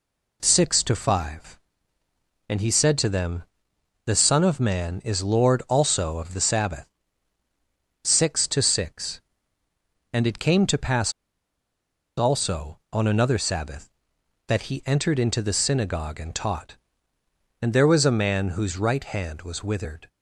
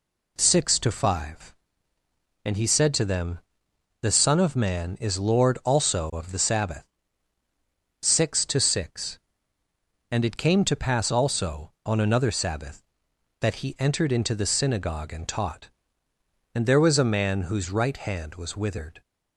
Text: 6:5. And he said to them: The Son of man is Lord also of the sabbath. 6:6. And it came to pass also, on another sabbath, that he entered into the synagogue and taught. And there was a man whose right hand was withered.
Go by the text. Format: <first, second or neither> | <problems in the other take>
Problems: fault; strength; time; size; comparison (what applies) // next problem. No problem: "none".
second | pauses between "pass" and "also"; at 11.1 s; 1.0 s long